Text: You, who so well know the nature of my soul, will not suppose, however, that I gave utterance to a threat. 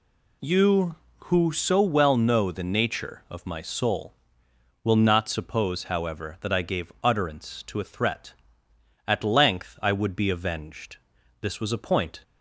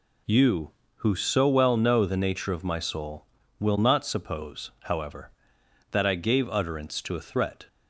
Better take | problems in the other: second | goes on to say "At length I would be avenged this was a point"; strong; from 9.0 s on; 3.1 s long

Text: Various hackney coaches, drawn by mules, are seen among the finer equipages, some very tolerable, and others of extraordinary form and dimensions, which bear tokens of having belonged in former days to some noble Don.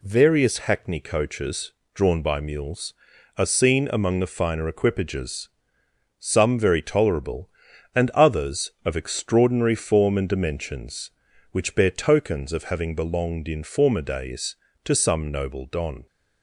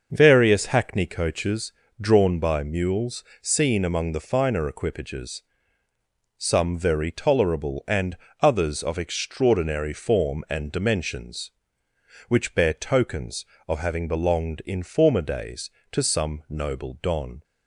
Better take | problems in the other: first | starts louder than the rest; until 1.1 s; 6 dB // skips "are"; at 3.3 s // pauses between "and" and "others"; slight; at 8.1 s; 0.24 s long

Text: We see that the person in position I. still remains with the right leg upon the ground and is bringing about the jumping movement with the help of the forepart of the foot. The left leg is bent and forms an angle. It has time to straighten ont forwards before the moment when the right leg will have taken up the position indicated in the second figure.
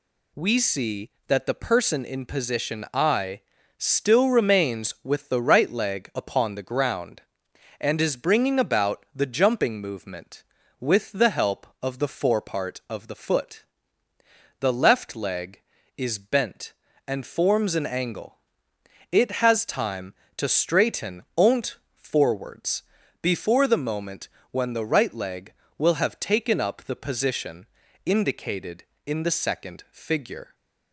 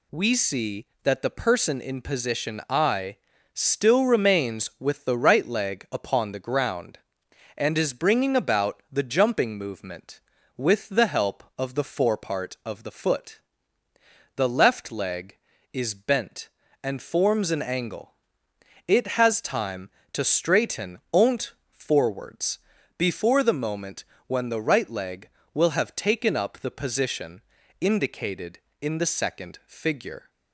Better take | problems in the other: neither | pauses between "ont" and "forwards"; slight; the same in both // pauses between "forwards" and "before"; the same in both // pauses between "moment" and "when"; slight; the same in both // pauses between "position" and "indicated"; the same in both

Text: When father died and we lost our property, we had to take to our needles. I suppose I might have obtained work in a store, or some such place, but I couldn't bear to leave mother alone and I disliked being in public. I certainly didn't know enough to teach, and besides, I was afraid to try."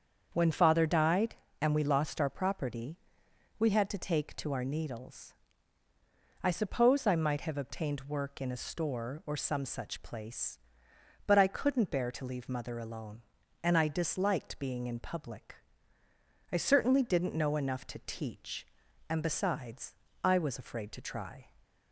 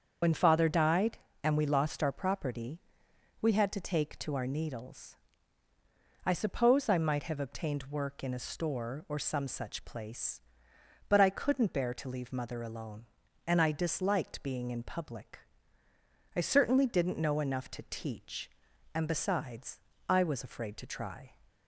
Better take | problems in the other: first | loses the start of "When"; at 0.2 s; 85 ms // starts louder than the rest; strong; until 1.4 s; 7 dB; also in the first

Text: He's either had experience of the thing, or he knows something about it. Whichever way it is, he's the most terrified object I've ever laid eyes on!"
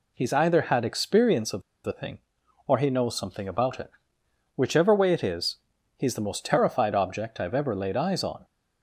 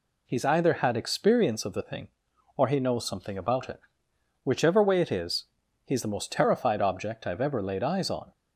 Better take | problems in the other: second | pauses between "of" and "the"; slight; at 1.6 s; 0.23 s long

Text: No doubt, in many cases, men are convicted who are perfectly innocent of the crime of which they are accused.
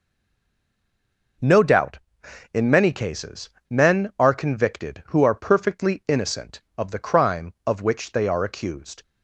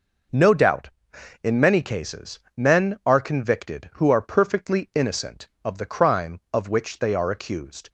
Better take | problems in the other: second | stays silent before the first word; noticeable; until 1.4 s; 1.4 s long

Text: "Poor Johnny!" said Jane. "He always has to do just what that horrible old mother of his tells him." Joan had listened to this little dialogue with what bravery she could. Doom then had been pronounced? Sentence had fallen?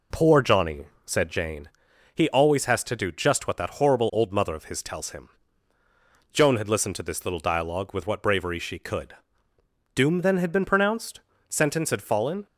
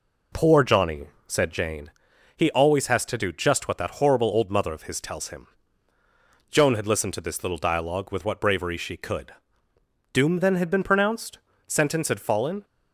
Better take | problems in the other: neither | none

